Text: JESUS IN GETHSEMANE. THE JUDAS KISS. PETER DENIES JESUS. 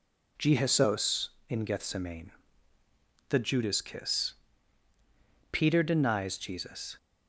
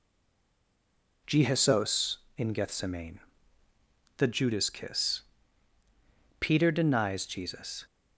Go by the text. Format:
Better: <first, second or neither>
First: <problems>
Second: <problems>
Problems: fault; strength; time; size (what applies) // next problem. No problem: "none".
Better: first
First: none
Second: stays silent before the first word; noticeable; until 1.2 s; 1.2 s long